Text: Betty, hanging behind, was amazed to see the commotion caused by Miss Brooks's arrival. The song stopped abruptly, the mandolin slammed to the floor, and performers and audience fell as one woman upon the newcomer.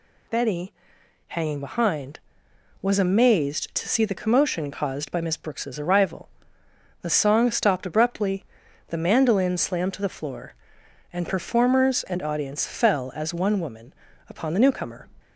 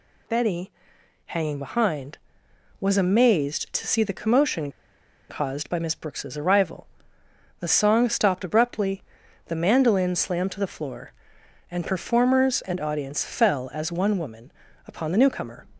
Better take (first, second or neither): first